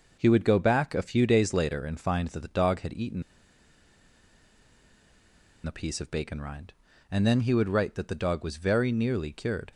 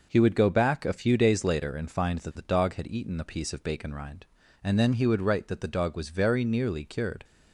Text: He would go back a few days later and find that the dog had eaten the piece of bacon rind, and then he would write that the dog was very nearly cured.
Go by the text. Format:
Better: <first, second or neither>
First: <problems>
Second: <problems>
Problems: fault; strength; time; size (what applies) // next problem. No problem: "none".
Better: second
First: pauses between "eaten" and "the"; strong; at 3.2 s; 2.4 s long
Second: none